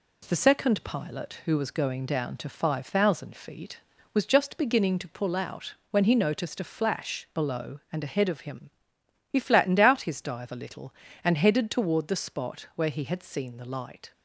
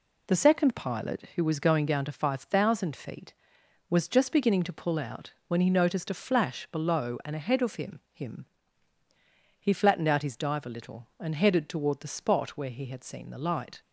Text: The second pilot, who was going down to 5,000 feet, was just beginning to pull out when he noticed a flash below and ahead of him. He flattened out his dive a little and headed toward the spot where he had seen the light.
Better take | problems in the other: first | pauses between "out" and "when"; slight; at 5.3 s; 0.16 s long; slight in the first // says "him" twice; at 8.1 s

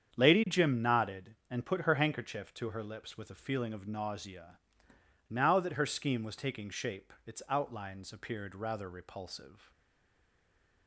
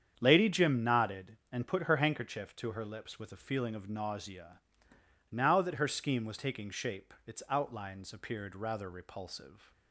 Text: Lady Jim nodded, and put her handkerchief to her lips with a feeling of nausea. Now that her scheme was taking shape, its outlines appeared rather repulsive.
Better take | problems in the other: second | starts louder than the rest; strong; until 1.2 s; 8 dB; strong in the second // stays silent after the last word; noticeable; from 9.7 s on; 1.1 s long

